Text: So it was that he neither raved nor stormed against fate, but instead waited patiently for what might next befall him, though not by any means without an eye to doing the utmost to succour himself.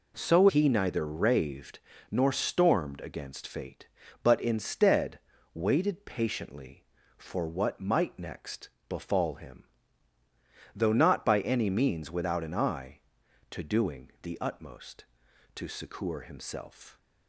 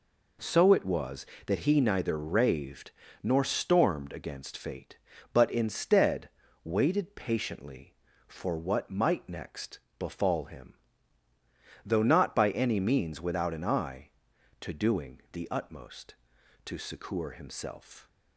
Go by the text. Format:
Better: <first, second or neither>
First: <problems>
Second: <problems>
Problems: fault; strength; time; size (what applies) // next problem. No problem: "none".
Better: second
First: skips "it was that"; at 0.4 s // pauses between "raved" and "nor"; slight; at 1.7 s; 0.30 s long // pauses between "instead" and "waited"; slight; at 5.1 s; 0.34 s long // pauses between "next" and "befall"; slight; at 8.6 s; 0.18 s long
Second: pauses between "raved" and "nor"; slight; at 2.9 s; 0.30 s long // pauses between "instead" and "waited"; slight; at 6.2 s; 0.34 s long // pauses between "next" and "befall"; slight; at 9.7 s; 0.18 s long